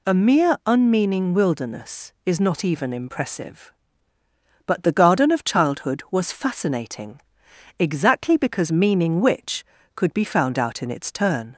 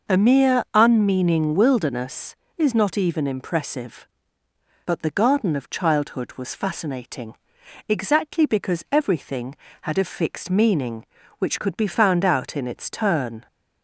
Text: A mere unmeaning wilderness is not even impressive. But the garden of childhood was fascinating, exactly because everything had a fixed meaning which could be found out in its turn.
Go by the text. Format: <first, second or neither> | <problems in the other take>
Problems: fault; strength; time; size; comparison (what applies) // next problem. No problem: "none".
second | skips "everything had a fixed"; at 8.7 s